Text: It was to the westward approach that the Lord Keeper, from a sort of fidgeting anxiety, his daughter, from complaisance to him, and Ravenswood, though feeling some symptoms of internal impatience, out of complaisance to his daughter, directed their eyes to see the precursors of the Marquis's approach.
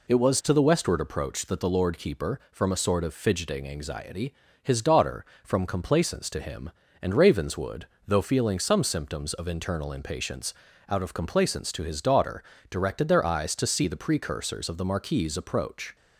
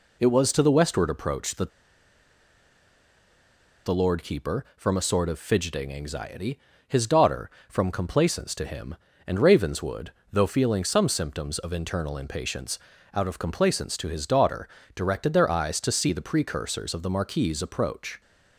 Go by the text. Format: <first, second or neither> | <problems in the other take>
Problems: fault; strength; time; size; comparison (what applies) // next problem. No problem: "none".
first | pauses between "that" and "the"; strong; at 1.6 s; 2.1 s long